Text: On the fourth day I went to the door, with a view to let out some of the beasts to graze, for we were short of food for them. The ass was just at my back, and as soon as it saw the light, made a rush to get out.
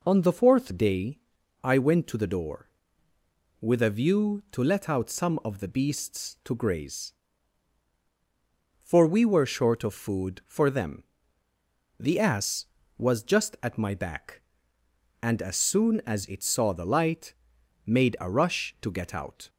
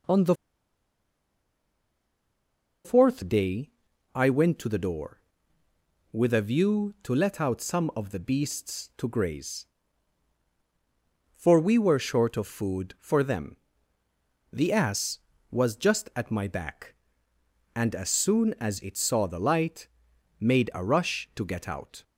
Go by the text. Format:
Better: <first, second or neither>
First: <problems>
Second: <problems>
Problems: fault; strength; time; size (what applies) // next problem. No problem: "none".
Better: first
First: pauses between "day" and "I"; at 1.1 s; 0.42 s long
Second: pauses between "the" and "fourth"; strong; at 0.3 s; 2.5 s long // pauses between "day" and "I"; at 3.7 s; 0.42 s long